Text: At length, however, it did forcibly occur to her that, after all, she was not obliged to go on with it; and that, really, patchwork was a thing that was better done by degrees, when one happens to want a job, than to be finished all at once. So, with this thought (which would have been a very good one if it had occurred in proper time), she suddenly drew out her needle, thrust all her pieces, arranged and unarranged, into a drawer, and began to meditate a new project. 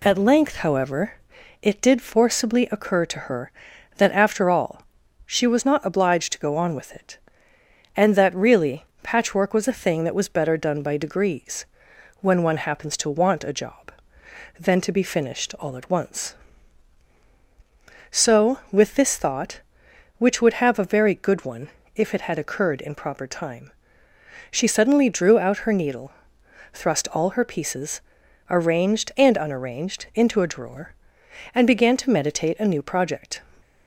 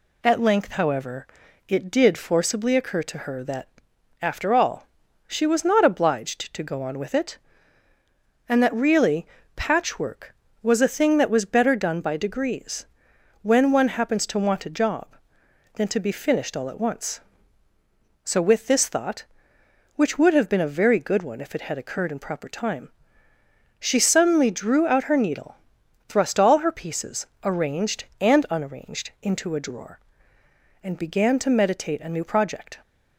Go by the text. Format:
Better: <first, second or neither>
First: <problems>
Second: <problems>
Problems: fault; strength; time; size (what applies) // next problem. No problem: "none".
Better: second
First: skips "been"; at 20.7 s // pauses between "one" and "if"; slight; at 21.6 s; 0.26 s long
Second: none